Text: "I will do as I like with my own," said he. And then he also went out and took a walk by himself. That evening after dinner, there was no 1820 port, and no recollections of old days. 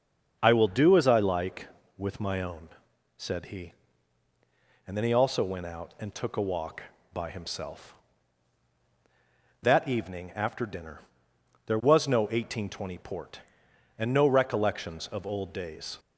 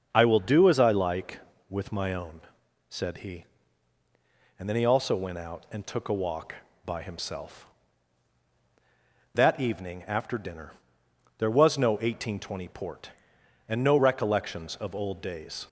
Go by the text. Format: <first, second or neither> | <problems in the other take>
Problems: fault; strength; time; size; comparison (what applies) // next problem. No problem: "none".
neither | starts louder than the rest; the same in both